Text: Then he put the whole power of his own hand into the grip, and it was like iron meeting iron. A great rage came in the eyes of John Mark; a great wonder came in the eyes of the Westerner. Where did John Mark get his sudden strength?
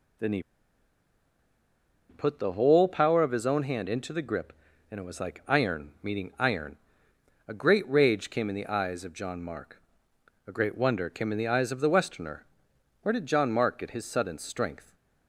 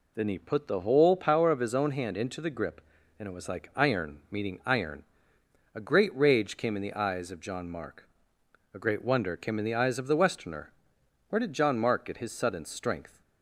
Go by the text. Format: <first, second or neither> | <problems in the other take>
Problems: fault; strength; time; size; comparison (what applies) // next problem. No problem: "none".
second | pauses between "he" and "put"; strong; at 0.4 s; 1.6 s long